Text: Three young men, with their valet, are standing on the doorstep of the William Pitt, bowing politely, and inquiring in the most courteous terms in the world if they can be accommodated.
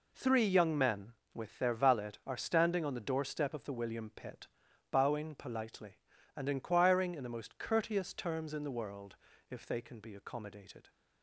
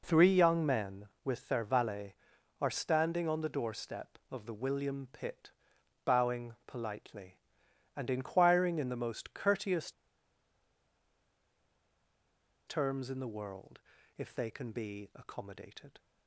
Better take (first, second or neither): first